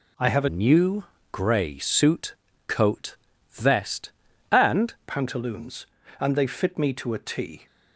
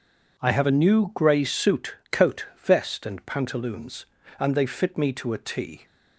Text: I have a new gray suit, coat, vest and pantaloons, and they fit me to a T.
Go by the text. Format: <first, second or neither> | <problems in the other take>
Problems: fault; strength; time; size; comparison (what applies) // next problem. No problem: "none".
second | changes voice from "new" to "and"; from 0.4 to 4.9 s; 4.5 s long // pauses between "new" and "gray"; slight; at 1.0 s; 0.26 s long